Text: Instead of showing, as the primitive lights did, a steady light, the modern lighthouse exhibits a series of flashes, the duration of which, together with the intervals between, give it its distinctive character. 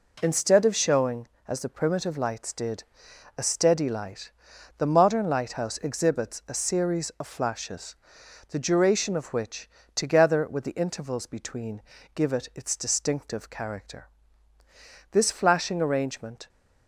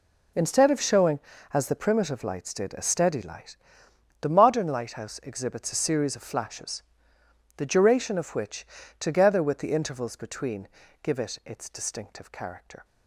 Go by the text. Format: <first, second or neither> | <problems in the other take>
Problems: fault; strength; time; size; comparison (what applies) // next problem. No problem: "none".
second | goes on to say "This flashing arrangement"; from 15.1 s on; 1.3 s long